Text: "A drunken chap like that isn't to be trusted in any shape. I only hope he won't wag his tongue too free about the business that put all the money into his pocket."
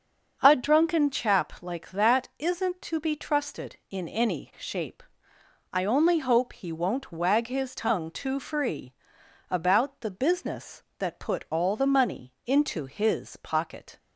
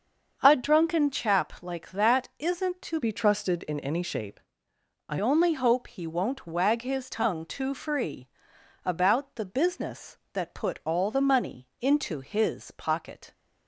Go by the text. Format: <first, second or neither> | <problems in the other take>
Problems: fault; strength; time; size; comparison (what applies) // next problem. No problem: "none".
first | starts louder than the rest; until 1.4 s; 6.5 dB; also in the first // changes voice from "be" to "I"; from 3.0 to 5.1 s; 2.1 s long // pauses between "free" and "about"; noticeable; at 8.2 s; 0.56 s long; noticeable in the first